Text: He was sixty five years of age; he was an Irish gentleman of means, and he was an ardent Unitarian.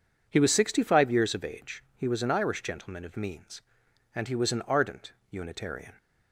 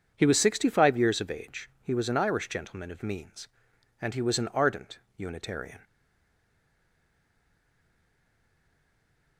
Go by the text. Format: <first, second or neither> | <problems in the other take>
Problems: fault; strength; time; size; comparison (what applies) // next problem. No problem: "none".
first | pauses between "ardent" and "Unitarian"; slight; at 4.9 s; 0.18 s long; slight in the first // stays silent after the last word; strong; from 5.8 s on; 3.5 s long